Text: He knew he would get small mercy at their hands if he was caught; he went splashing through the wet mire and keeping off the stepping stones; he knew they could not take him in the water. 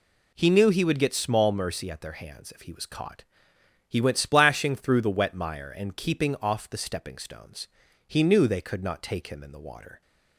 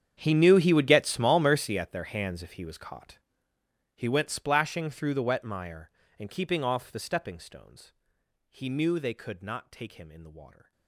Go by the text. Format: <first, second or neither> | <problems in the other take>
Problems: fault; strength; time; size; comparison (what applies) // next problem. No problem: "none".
first | gets quieter; strong; throughout; 20.5 dB